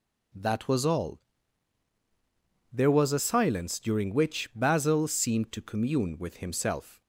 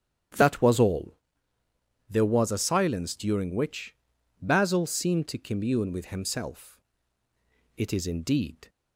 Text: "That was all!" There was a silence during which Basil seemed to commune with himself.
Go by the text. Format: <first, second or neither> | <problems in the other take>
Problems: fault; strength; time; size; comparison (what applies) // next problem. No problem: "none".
first | starts louder than the rest; strong; until 2.2 s; 9.5 dB // pauses between "which" and "Basil"; noticeable; at 3.9 s; 0.46 s long // goes on to say "It is indeed"; noticeable; from 7.7 s on; 0.92 s long